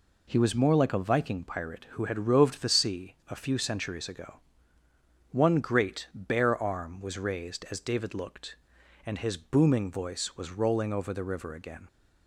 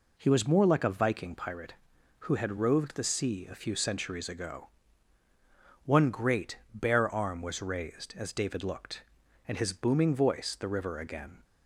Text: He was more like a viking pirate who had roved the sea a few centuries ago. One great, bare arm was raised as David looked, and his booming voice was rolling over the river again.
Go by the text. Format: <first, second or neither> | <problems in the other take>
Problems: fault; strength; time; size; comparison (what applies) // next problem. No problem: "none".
first | skips "was rolling over"; at 10.5 s